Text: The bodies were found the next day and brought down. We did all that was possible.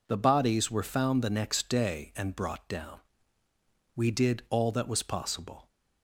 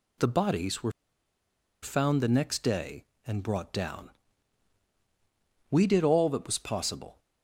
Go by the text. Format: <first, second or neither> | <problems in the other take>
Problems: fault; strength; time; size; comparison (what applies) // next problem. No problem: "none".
first | pauses between "were" and "found"; noticeable; at 0.9 s; 0.90 s long